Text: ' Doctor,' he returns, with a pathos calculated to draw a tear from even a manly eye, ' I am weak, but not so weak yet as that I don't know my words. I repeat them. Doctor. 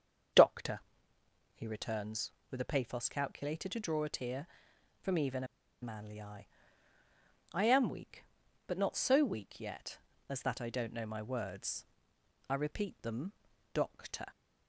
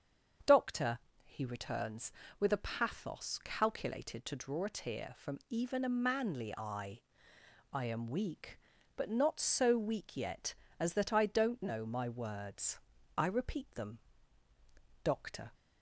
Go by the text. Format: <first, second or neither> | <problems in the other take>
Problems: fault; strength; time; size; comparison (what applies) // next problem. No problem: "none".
second | starts louder than the rest; strong; until 2.0 s; 7 dB; also in the second // pauses between "a" and "manly"; at 5.4 s; 0.36 s long